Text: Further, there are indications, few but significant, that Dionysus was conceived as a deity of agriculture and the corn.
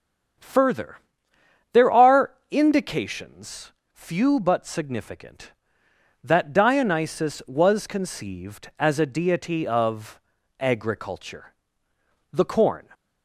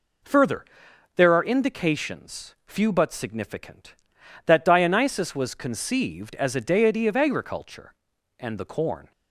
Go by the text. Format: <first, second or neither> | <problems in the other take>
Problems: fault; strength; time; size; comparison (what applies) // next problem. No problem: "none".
second | starts louder than the rest; strong; until 2.1 s; 7.5 dB // pauses between "are" and "indications"; slight; at 2.3 s; 0.16 s long // pauses between "of" and "agriculture"; at 10.1 s; 0.40 s long // skips "and"; at 11.9 s